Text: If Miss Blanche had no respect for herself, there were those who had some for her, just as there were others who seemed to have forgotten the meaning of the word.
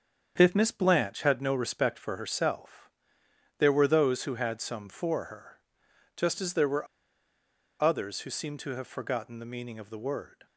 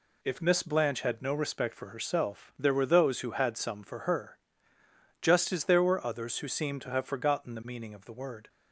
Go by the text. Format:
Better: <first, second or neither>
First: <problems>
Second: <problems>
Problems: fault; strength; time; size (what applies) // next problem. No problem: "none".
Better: second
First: starts louder than the rest; strong; until 1.3 s; 7.5 dB // pauses between "were" and "others"; noticeable; at 6.8 s; 0.96 s long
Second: none